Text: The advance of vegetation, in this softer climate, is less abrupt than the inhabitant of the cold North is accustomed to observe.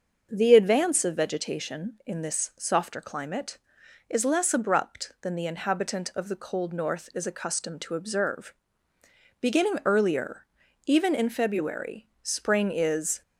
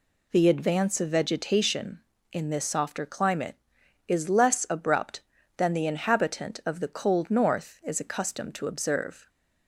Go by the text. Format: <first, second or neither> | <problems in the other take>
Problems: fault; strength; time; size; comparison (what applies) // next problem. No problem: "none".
second | starts louder than the rest; until 1.3 s; 6.5 dB // goes on to say "Beginning earlier even in February Spring is"; strong; from 9.3 s on; 3.8 s long